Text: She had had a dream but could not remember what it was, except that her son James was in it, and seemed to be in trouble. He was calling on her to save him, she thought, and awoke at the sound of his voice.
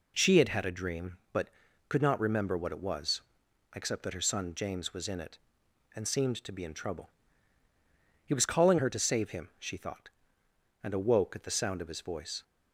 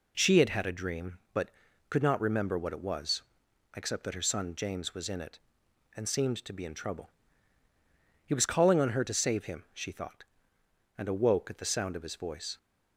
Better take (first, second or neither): second